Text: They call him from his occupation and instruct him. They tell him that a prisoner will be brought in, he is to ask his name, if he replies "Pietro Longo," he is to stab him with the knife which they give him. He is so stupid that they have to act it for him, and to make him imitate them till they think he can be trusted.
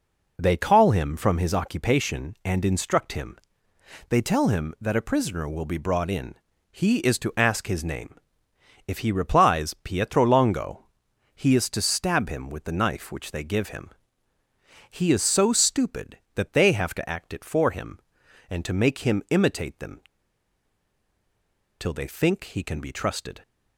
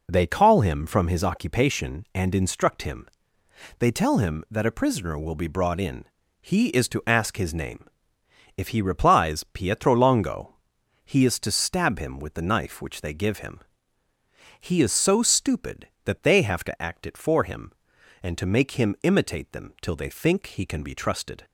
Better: second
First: pauses between "them" and "till"; strong; at 20.0 s; 1.7 s long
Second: none

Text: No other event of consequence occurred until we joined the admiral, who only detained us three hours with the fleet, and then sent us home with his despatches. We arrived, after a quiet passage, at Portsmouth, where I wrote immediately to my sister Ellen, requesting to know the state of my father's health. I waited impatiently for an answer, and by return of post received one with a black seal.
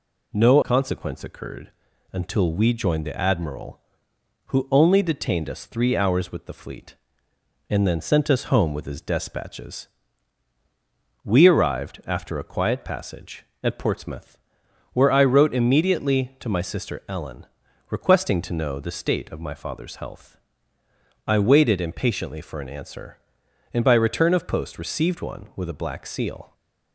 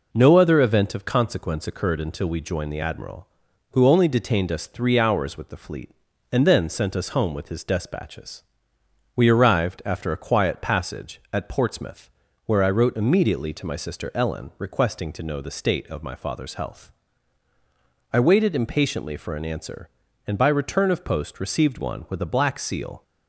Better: second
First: skips "other event of"; at 0.6 s // pauses between "occurred" and "until"; at 1.7 s; 0.42 s long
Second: none

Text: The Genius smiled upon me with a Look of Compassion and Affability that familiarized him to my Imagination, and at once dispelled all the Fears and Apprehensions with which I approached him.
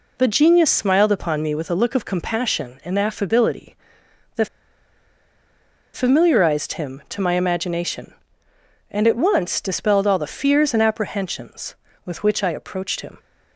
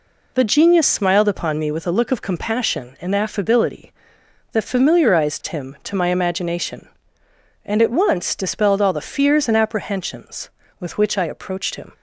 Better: second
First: pauses between "that" and "familiarized"; strong; at 4.4 s; 1.4 s long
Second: none

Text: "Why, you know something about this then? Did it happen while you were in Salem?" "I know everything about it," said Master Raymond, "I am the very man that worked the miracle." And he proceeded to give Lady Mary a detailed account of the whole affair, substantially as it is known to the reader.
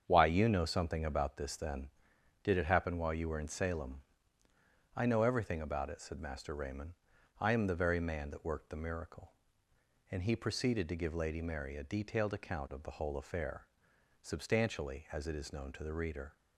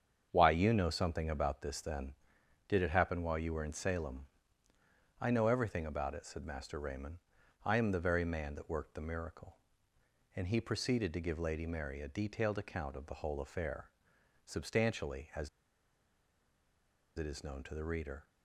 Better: first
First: starts louder than the rest; strong; until 1.0 s; 7.5 dB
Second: starts louder than the rest; strong; until 1.3 s; 7.5 dB // pauses between "as" and "it"; strong; at 15.4 s; 1.6 s long

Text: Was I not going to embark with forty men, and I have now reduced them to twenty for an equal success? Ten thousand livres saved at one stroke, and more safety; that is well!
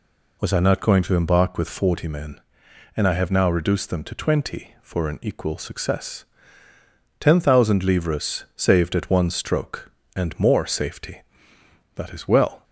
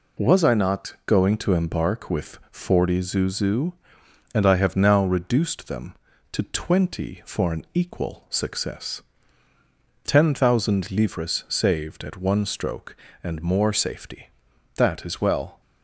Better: first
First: none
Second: says "zuzu" for "men"; at 3.0 s

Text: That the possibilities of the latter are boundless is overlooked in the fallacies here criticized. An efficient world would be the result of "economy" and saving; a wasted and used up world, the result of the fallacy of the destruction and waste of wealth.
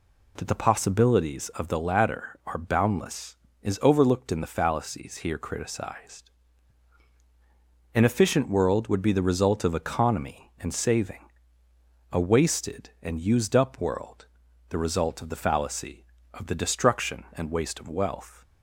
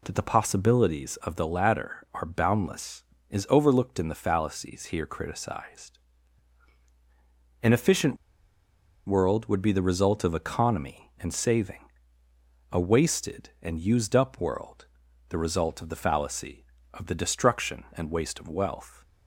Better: first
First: none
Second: pauses between "efficient" and "world"; noticeable; at 8.1 s; 0.90 s long

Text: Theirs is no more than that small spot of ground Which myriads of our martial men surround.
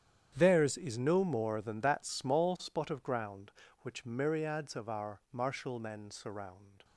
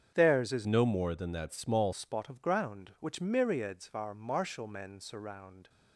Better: first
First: starts louder than the rest; strong; until 1.3 s; 9 dB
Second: starts louder than the rest; strong; until 1.1 s; 8 dB // changes voice from "no" to "small"; from 0.6 to 1.9 s; 1.3 s long

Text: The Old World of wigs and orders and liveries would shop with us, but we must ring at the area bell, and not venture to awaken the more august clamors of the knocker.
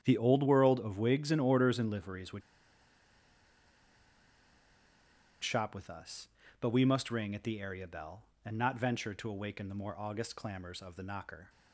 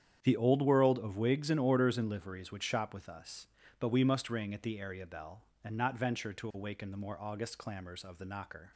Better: second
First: starts louder than the rest; strong; until 1.0 s; 8.5 dB // pauses between "would" and "shop"; strong; at 2.4 s; 3.0 s long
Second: starts louder than the rest; strong; until 1.2 s; 8.5 dB

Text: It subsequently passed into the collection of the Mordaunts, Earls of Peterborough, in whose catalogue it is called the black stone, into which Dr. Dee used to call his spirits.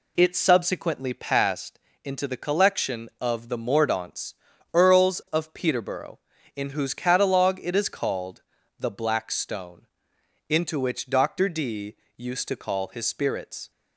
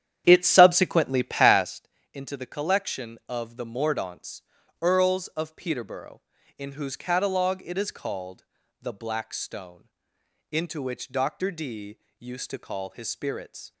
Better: first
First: pauses between "passed" and "into"; slight; at 1.7 s; 0.24 s long // pauses between "called" and "the"; slight; at 8.4 s; 0.36 s long // pauses between "Dee" and "used"; slight; at 11.9 s; 0.20 s long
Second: starts louder than the rest; strong; until 1.8 s; 10 dB // pauses between "passed" and "into"; slight; at 1.8 s; 0.24 s long // pauses between "called" and "the"; slight; at 8.4 s; 0.36 s long // pauses between "Dee" and "used"; slight; at 11.9 s; 0.20 s long

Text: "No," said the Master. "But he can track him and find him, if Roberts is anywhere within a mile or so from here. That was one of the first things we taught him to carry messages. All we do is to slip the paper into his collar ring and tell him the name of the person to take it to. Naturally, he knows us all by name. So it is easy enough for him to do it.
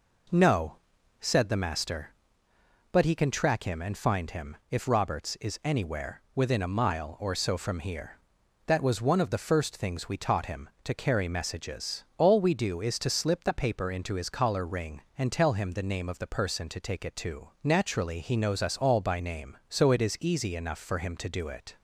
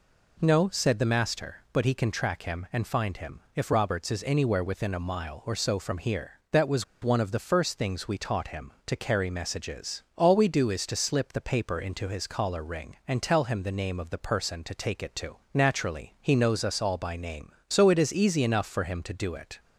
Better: first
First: none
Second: pauses between "was" and "one"; slight; at 6.8 s; 0.19 s long

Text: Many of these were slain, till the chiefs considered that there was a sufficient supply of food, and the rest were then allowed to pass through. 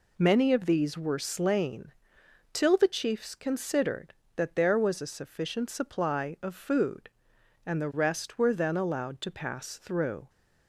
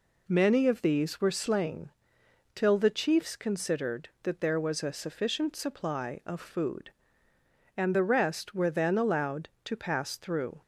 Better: neither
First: none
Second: none

